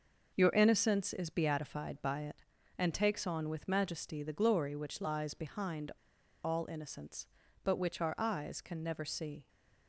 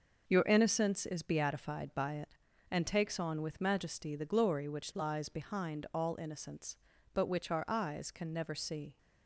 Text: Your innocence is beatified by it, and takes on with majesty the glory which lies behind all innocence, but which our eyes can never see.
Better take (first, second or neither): second